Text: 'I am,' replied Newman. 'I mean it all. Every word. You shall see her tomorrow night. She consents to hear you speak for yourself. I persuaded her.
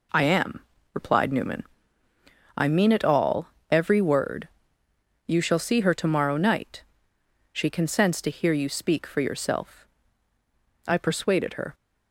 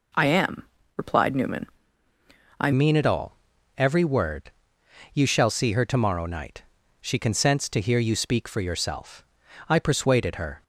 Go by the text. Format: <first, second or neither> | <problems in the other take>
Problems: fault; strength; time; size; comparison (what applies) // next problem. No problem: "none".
first | changes voice at "mean"; from 2.7 s on; 7.9 s long